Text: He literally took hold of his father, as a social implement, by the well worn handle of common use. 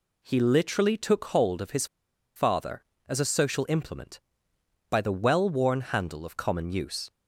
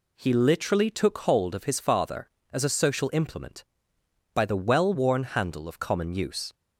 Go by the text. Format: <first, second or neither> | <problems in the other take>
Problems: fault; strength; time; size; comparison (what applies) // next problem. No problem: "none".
second | pauses between "his" and "father"; noticeable; at 1.8 s; 0.50 s long